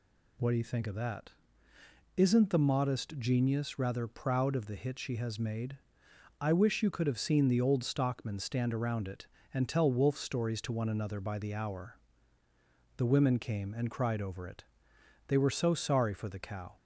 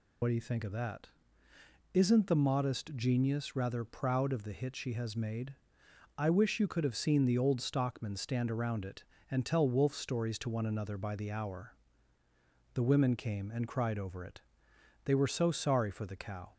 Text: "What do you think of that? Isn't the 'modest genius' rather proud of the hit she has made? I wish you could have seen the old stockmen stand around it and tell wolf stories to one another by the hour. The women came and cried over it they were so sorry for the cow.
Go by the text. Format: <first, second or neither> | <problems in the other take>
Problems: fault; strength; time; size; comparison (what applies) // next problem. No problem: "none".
first | loses the start of "What"; at 0.2 s; 60 ms // pauses between "it" and "they"; noticeable; at 14.3 s; 0.64 s long; noticeable in the first